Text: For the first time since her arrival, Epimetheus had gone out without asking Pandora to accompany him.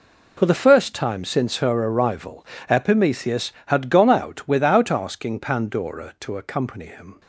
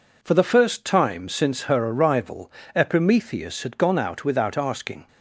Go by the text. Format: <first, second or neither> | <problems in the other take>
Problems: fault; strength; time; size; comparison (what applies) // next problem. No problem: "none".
first | stops before "Pandora to accompany him"; at 5.0 s